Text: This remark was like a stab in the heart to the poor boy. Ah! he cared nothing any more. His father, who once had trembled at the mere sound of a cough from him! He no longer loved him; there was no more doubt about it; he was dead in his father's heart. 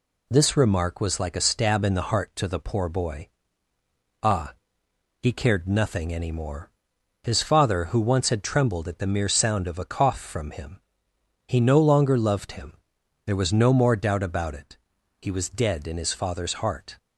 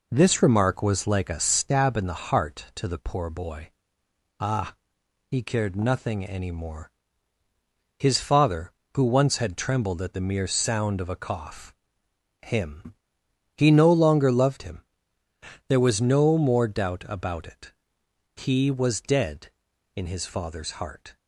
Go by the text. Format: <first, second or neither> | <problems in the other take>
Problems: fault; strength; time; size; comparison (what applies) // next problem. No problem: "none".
first | skips "from"; at 12.0 s